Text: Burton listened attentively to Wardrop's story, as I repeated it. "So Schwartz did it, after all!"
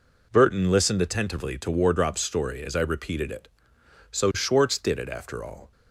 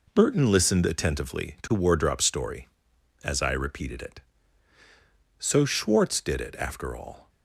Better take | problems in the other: neither | none

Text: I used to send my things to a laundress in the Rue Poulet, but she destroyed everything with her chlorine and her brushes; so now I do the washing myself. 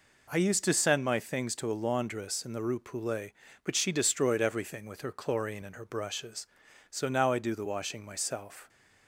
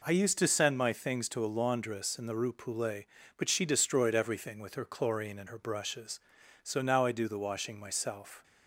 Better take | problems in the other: neither | none

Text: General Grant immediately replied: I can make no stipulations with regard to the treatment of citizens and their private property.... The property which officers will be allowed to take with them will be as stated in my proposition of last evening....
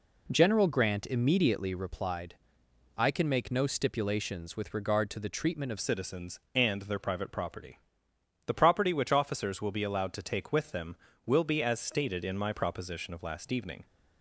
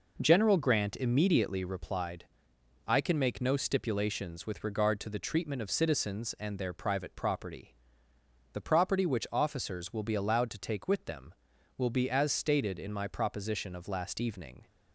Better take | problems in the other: second | changes voice at "citizens"; from 5.7 s on; 8.1 s long

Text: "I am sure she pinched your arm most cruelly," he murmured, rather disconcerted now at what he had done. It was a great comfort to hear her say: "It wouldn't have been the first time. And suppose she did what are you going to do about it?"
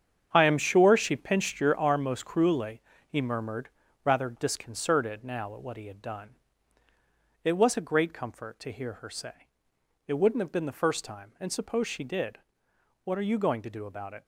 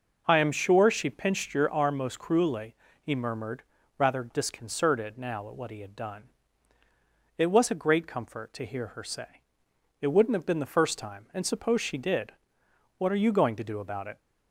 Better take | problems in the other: second | gets quieter; strong; throughout; 10 dB // pauses between "did" and "what"; noticeable; at 12.3 s; 0.64 s long; noticeable in the second

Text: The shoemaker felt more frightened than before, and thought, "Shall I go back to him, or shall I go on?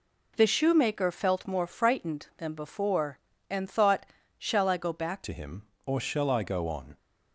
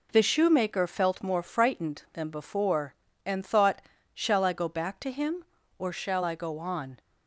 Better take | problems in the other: second | changes voice at "to"; from 5.2 s on; 1.7 s long

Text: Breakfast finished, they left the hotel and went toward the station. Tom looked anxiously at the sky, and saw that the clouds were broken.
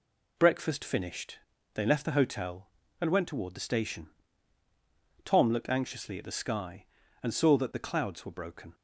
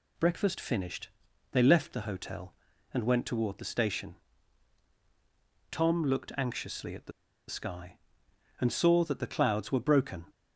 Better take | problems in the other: first | pauses between "the" and "sky"; at 7.1 s; 0.36 s long

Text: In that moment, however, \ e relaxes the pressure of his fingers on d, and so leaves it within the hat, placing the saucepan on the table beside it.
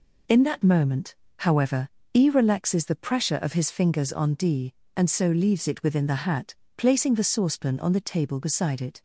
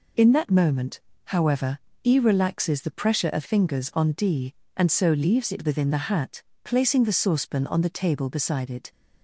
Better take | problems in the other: first | skips "his"; at 3.4 s

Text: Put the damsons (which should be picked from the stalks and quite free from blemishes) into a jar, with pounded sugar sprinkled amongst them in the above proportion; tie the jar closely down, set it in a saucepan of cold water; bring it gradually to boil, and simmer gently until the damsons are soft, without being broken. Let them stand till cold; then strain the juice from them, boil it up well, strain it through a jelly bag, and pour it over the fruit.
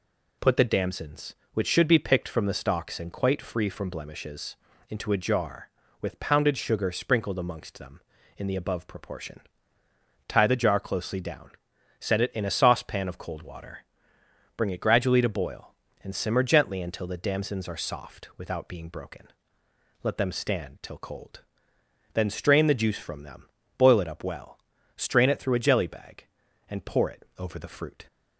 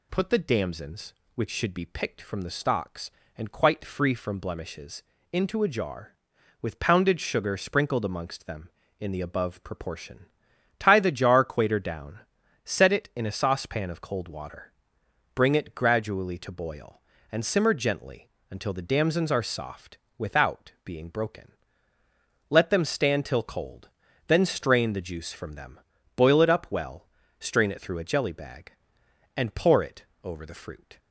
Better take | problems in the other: first | says "quater" for "closely"; at 11.4 s // pauses between "gently" and "until"; slight; at 18.2 s; 0.22 s long // pauses between "it" and "over"; slight; at 30.0 s; 0.20 s long

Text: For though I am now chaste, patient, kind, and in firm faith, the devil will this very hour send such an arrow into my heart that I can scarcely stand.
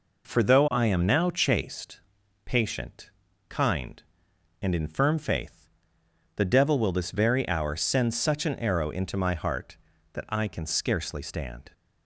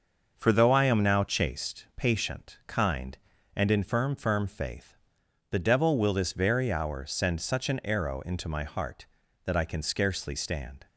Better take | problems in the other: first | starts louder than the rest; noticeable; until 1.3 s; 6 dB // says "firm" twice; at 4.1 s

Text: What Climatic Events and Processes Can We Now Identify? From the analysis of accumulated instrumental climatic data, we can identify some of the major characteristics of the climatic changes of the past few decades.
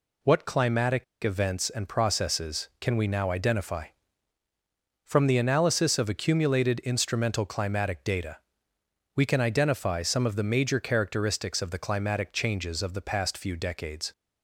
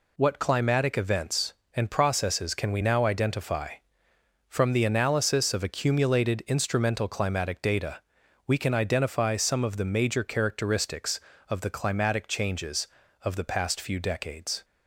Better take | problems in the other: second | pauses between "Climatic" and "Events"; slight; at 1.0 s; 0.19 s long

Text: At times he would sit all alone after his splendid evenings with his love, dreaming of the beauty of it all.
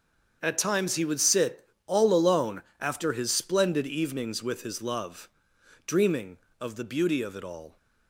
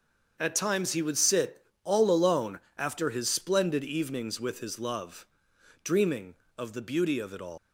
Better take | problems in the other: first | starts louder than the rest; until 1.4 s; 7 dB; also in the first // pauses between "sit" and "all"; slight; at 1.6 s; 0.18 s long; slight in the first // pauses between "alone" and "after"; slight; at 2.5 s; 0.18 s long; slight in the first // leaves "all" unfinished; at 7.5 s; 150 ms

